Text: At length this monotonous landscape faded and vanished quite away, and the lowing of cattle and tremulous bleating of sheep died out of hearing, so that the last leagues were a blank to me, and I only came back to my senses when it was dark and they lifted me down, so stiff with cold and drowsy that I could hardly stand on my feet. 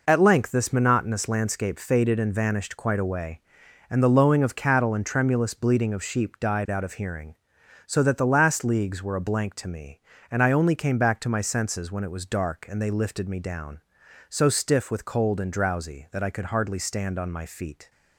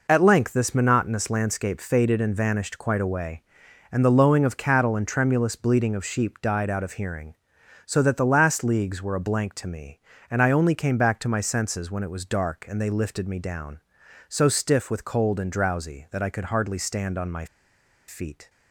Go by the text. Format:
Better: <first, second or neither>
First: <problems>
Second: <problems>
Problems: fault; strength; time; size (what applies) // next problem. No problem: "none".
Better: first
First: none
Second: pauses between "my" and "feet"; noticeable; at 17.4 s; 0.62 s long